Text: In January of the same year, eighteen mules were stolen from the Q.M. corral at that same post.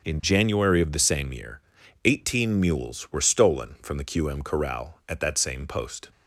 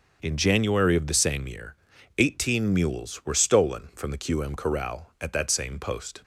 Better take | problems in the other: neither | starts louder than the rest; the same in both

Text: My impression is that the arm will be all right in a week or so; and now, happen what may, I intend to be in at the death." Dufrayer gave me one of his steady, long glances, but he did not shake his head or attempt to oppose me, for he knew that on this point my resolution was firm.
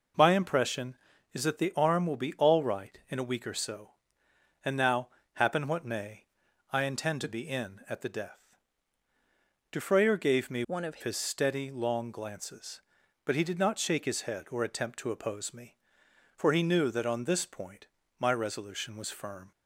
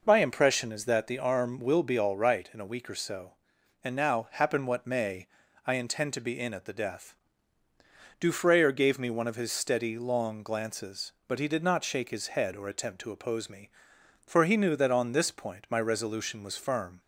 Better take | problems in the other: second | changes voice from "one" to "of"; from 10.6 to 11.0 s; 0.4 s long // pauses between "point" and "my"; slight; at 17.8 s; 0.34 s long

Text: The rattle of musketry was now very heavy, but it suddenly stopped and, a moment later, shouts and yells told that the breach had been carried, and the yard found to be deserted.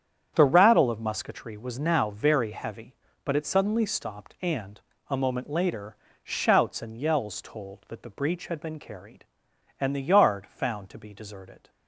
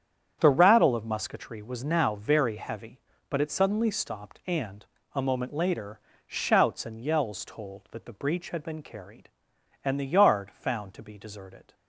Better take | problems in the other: neither | starts louder than the rest; strong; the same in both

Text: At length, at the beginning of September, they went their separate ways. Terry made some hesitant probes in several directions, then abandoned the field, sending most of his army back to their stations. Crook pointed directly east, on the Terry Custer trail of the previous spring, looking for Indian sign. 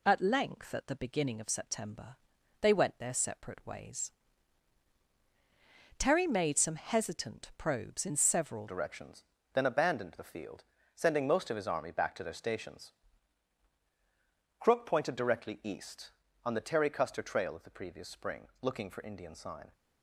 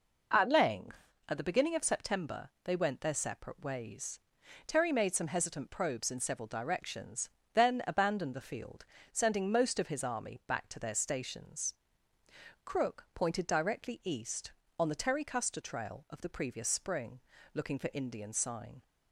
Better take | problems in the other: second | changes voice at "directions"; from 8.6 s on; 11.1 s long

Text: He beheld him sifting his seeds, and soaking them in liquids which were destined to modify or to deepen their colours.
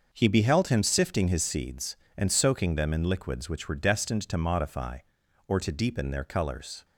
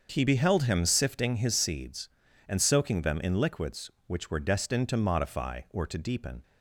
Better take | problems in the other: first | starts louder than the rest; until 1.1 s; 7 dB; noticeable in the first // stops before "their colours"; at 6.4 s

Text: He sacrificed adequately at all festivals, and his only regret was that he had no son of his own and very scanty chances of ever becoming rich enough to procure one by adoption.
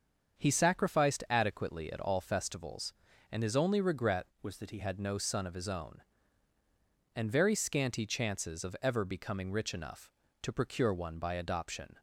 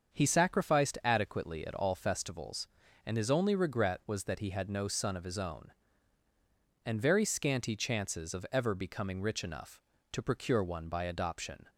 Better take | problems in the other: second | starts louder than the rest; until 1.4 s; 7 dB; also in the second // changes voice from "was" to "he"; from 4.4 to 4.7 s; 0.3 s long

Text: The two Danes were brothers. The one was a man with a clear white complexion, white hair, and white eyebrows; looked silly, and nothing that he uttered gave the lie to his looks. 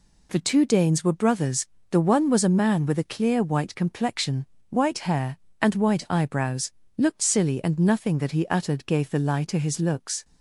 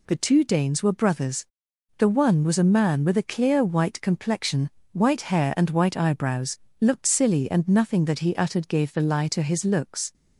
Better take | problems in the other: neither | none

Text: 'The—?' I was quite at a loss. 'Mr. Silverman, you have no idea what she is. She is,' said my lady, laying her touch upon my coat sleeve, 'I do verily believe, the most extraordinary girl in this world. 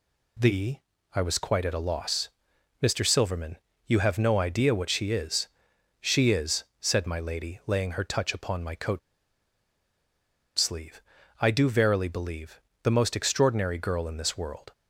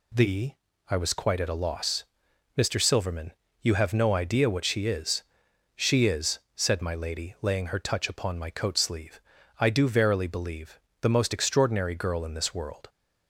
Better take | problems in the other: second | pauses between "coat" and "sleeve"; strong; at 8.9 s; 1.5 s long

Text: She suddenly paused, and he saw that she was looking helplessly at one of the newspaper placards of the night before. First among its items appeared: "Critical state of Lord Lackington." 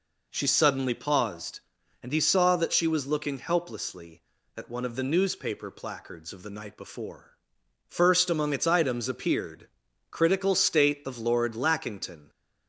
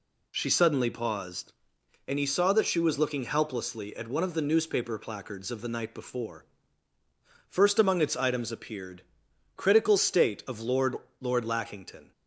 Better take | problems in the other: first | says "Lord" twice; at 11.1 s

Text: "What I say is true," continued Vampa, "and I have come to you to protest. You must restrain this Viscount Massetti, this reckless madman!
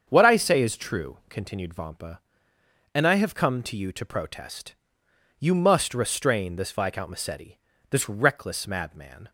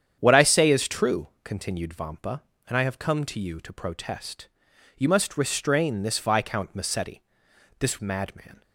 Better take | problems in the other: first | starts louder than the rest; strong; until 1.1 s; 8.5 dB; also in the first // skips "reckless"; at 7.9 s

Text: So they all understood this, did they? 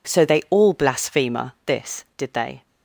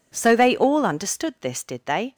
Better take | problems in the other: second | says "blasphemer" for "understood"; at 0.7 s

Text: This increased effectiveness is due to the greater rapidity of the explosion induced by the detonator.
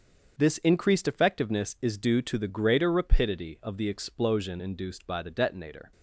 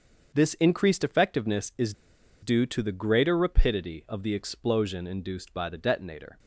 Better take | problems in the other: first | starts louder than the rest; until 1.3 s; 7 dB; also in the first // pauses between "is" and "due"; noticeable; at 1.9 s; 0.50 s long

